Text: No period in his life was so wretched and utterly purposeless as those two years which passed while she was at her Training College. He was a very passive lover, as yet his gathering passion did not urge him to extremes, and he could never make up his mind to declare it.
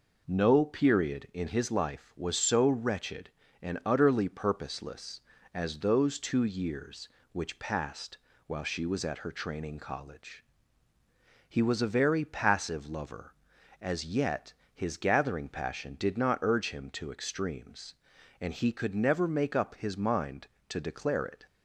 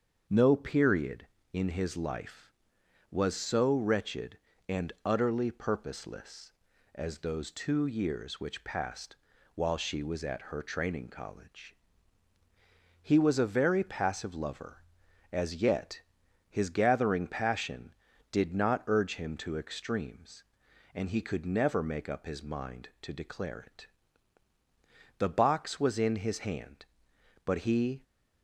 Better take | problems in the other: first | starts louder than the rest; until 1.5 s; 7 dB // pauses between "passed" and "while"; at 9.1 s; 0.40 s long; slight in the first // pauses between "yet" and "his"; noticeable; at 16.0 s; 0.48 s long; slight in the first // goes on to say "The box was in his hand but he"; strong; from 25.1 s on; 2.8 s long

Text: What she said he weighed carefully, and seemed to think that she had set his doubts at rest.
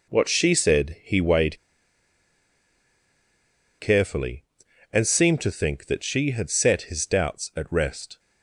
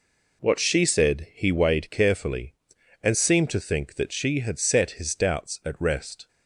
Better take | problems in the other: second | pauses between "weighed" and "carefully"; strong; at 1.5 s; 2.2 s long

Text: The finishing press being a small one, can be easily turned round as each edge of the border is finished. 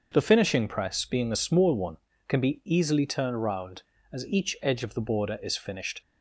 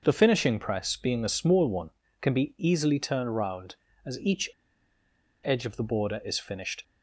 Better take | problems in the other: first | starts louder than the rest; noticeable; until 1.0 s; 6 dB; also in the first // pauses between "each" and "edge"; noticeable; at 4.4 s; 0.93 s long

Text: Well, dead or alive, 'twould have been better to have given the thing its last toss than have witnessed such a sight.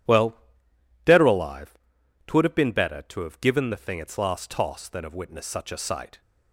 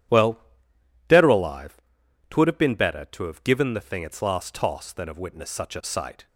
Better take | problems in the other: neither | none

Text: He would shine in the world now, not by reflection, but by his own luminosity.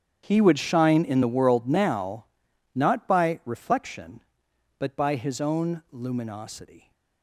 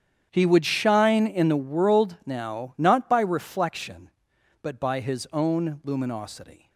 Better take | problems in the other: neither | starts louder than the rest; strong; the same in both

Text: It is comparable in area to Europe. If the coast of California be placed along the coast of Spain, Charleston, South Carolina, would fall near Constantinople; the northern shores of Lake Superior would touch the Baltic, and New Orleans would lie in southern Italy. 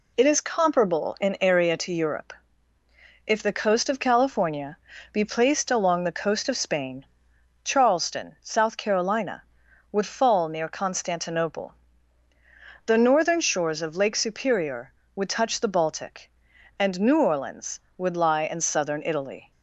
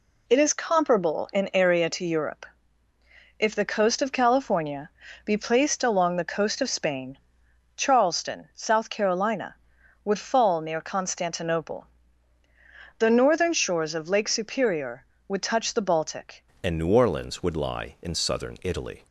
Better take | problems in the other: first | pauses between "California" and "be"; slight; at 4.9 s; 0.34 s long; slight in the first // changes voice at "and"; from 16.6 s on; 2.4 s long

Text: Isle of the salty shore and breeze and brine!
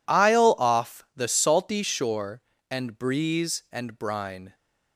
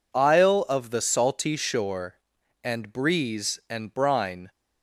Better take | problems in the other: second | says "off" for "of"; at 0.5 s

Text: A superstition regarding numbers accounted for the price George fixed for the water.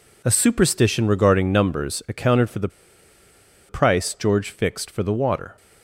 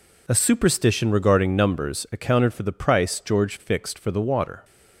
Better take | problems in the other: second | pauses between "the" and "price"; at 2.6 s; 1.0 s long

